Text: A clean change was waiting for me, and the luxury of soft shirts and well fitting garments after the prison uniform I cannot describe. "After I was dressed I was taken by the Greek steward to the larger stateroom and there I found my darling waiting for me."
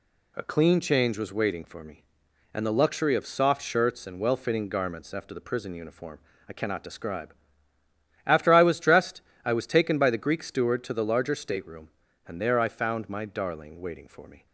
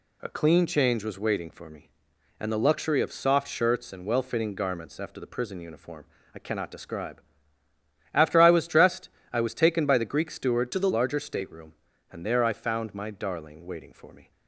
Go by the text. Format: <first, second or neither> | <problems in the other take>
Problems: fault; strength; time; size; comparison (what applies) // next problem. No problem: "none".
first | pauses between "uniform" and "I"; slight; at 6.0 s; 0.30 s long; slight in the first // pauses between "dressed" and "I"; slight; at 9.0 s; 0.24 s long; slight in the first // changes voice from "to" to "the"; from 10.7 to 10.8 s; 0.1 s long